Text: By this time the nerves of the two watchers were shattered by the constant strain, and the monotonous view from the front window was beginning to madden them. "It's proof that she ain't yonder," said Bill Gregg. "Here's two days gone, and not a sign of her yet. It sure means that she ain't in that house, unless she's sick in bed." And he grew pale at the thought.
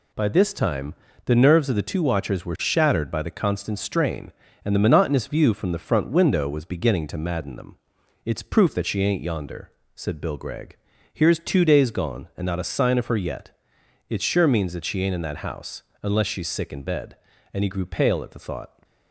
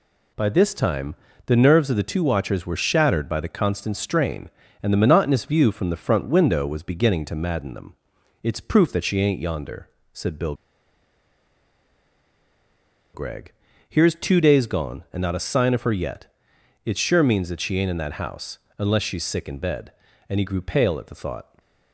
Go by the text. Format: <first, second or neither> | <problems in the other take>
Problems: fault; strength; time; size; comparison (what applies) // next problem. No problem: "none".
first | pauses between "time" and "the"; slight; at 1.1 s; 0.30 s long; slight in the first // pauses between "Bill" and "Gregg"; strong; at 10.5 s; 2.5 s long